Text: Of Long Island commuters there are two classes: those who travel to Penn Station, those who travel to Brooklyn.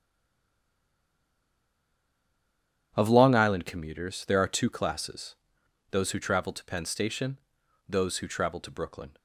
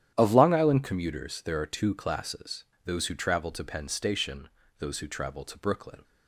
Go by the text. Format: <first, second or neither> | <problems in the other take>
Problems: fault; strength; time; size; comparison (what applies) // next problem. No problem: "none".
second | stays silent before the first word; strong; until 2.9 s; 2.9 s long // starts louder than the rest; strong; until 3.9 s; 9.5 dB; strong in the second